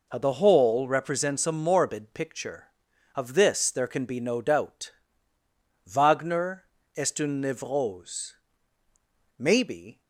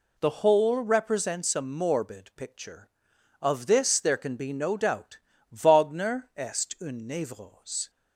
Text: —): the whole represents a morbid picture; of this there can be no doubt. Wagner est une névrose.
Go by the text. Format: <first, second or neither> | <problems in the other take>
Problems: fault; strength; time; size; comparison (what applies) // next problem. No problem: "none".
second | pauses between "Wagner" and "est"; slight; at 6.6 s; 0.32 s long // goes on to say "Maybe"; noticeable; from 9.3 s on; 0.64 s long